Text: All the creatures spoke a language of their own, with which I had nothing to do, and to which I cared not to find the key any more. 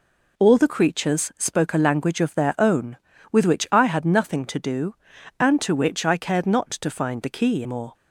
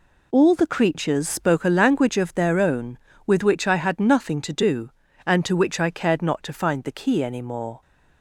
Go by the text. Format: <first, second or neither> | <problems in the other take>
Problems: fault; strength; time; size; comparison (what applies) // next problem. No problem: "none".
second | skips "any"; at 7.6 s